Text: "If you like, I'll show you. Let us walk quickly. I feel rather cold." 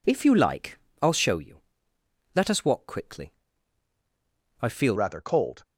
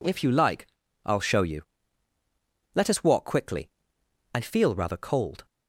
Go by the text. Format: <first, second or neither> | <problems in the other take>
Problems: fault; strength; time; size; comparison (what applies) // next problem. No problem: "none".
second | changes voice at "rather"; from 4.9 s on; 0.7 s long